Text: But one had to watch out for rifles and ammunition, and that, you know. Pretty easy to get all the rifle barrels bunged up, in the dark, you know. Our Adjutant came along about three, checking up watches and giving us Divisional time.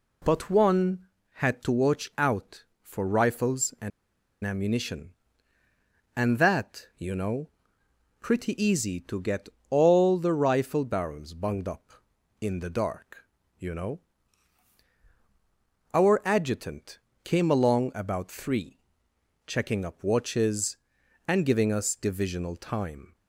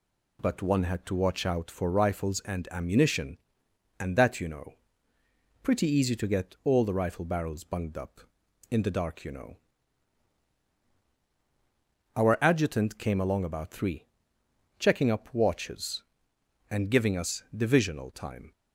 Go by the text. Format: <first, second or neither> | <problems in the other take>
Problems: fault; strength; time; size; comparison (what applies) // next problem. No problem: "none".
second | pauses between "and" and "ammunition"; noticeable; at 3.9 s; 0.54 s long // pauses between "get" and "all"; slight; at 9.4 s; 0.20 s long // pauses between "Adjutant" and "came"; slight; at 16.9 s; 0.24 s long